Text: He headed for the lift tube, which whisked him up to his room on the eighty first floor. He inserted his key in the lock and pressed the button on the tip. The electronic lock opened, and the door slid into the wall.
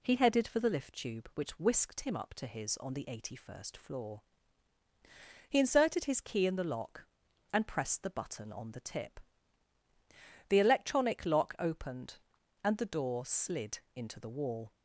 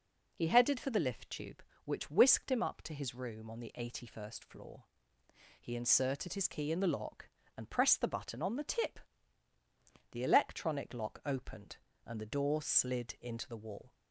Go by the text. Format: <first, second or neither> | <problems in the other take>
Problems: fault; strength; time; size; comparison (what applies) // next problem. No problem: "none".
second | skips "room"; at 2.7 s // pauses between "slid" and "into"; slight; at 13.7 s; 0.16 s long